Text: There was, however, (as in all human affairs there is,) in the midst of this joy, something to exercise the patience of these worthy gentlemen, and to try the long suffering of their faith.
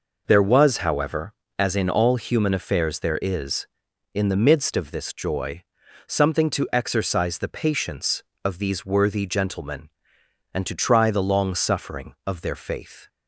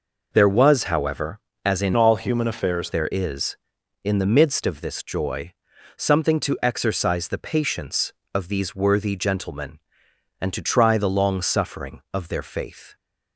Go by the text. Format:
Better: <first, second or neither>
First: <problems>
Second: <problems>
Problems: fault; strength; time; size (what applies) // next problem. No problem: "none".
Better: first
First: none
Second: changes voice from "all" to "affairs"; from 1.9 to 2.8 s; 0.9 s long